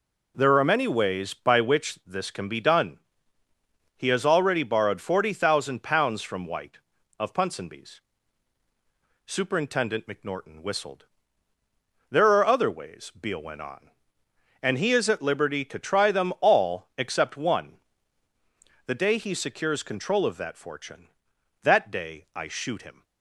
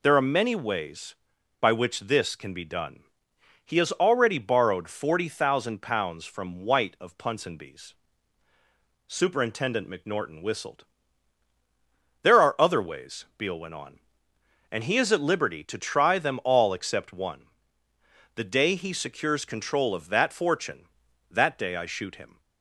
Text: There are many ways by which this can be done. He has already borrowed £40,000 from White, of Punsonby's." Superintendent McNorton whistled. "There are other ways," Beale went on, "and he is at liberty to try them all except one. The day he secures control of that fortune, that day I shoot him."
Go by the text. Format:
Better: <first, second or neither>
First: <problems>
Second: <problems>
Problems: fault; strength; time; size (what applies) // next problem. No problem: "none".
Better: neither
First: none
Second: none